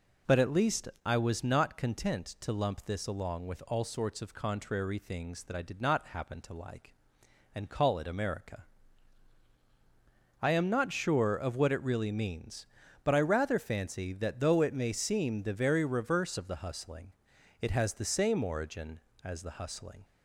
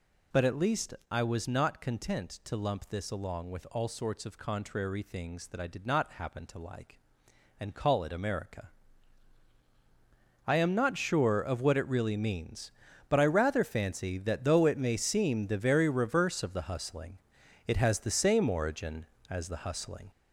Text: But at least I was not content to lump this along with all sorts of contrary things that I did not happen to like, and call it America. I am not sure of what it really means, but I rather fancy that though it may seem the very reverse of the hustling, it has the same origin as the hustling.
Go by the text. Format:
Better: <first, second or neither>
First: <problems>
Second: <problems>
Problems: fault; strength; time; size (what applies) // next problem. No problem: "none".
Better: first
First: pauses between "least" and "I"; slight; at 0.8 s; 0.18 s long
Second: gets louder; noticeable; throughout; 5 dB // pauses between "least" and "I"; slight; at 0.9 s; 0.18 s long